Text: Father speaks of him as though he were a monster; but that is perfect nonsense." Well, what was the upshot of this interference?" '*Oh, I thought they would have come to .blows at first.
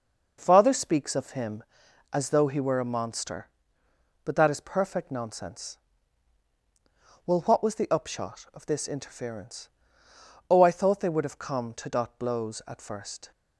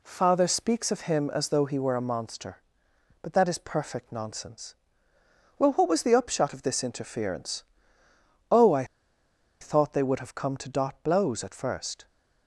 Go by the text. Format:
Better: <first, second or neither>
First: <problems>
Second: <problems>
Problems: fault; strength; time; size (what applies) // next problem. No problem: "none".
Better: first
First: none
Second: pauses between "I" and "thought"; noticeable; at 8.8 s; 0.75 s long